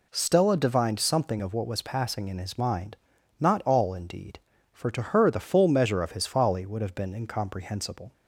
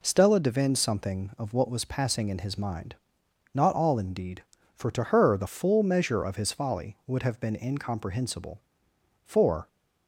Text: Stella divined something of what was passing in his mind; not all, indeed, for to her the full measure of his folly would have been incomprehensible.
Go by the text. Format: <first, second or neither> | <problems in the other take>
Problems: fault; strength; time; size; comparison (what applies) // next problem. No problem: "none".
first | goes on to say "For"; slight; from 9.2 s on; 0.42 s long